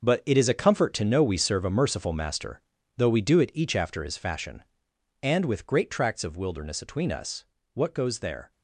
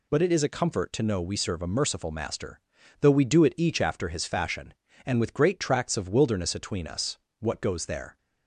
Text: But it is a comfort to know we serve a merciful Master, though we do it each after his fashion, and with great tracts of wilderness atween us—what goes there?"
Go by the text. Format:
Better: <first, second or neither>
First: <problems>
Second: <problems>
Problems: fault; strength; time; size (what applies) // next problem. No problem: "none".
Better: second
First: gets quieter; strong; throughout; 11 dB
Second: none